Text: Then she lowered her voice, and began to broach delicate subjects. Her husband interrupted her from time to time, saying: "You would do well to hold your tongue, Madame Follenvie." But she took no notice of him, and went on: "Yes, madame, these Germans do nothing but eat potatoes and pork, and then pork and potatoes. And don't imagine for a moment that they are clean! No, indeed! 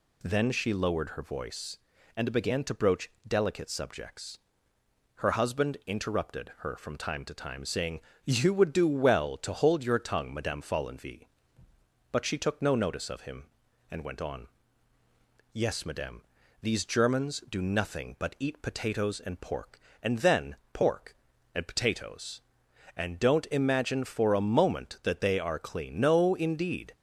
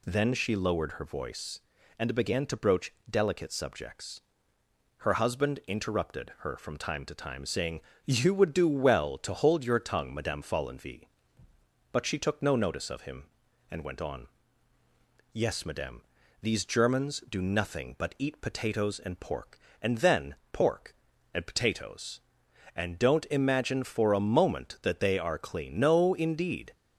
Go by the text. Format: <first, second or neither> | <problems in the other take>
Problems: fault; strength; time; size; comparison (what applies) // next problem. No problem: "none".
neither | pauses between "broach" and "delicate"; slight; the same in both // pauses between "then" and "pork"; slight; the same in both